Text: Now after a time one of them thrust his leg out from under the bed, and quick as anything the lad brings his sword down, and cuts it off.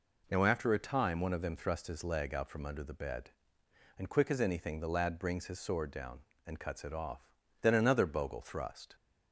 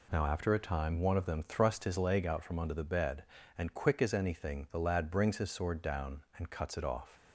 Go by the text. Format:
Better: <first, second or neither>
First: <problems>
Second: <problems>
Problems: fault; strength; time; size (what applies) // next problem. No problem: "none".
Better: second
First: goes on to say "Then another bogle thrust"; from 7.6 s on; 1.3 s long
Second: none